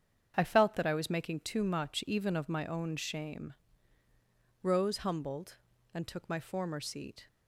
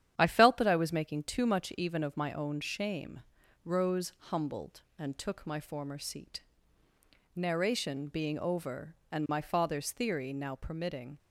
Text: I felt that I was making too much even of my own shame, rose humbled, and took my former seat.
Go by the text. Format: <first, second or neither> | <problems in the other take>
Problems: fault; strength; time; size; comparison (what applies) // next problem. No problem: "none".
first | starts louder than the rest; strong; until 1.2 s; 10 dB; strong in the first // pauses between "rose" and "humbled"; slight; at 4.1 s; 0.16 s long // goes on to say "Narration being over and my father's theory now permitting"; strong; from 7.3 s on; 3.8 s long